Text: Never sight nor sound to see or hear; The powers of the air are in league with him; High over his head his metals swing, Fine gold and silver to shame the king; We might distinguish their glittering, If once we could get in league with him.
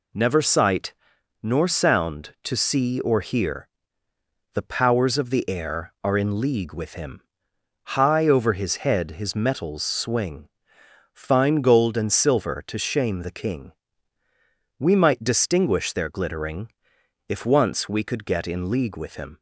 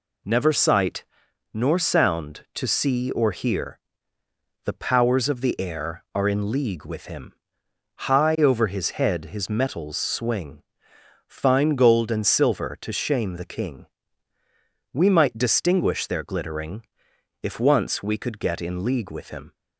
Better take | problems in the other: neither | pauses between "sight" and "nor"; noticeable; the same in both

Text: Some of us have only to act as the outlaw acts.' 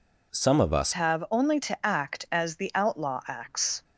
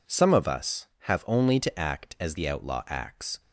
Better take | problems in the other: second | changes voice at "have"; from 0.9 s on; 2.9 s long

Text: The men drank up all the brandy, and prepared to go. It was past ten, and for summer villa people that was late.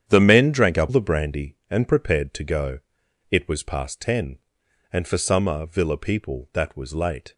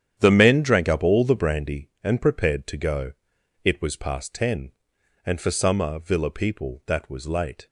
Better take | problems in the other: second | starts louder than the rest; strong; until 1.1 s; 9 dB; strong in the second // skips "all"; at 0.9 s

